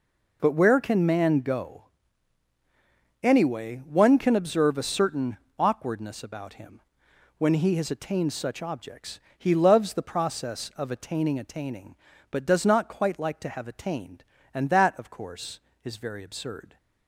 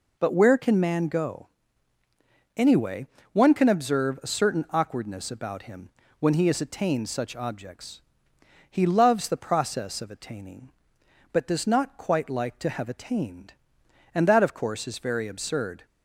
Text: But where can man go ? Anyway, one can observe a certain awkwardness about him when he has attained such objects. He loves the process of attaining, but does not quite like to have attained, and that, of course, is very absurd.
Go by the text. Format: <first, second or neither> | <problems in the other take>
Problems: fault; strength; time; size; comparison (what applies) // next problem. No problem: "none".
second | pauses between "certain" and "awkwardness"; slight; at 5.3 s; 0.22 s long // pauses between "him" and "when"; noticeable; at 6.8 s; 0.56 s long; slight in the second // says "attaining" twice; at 11.3 s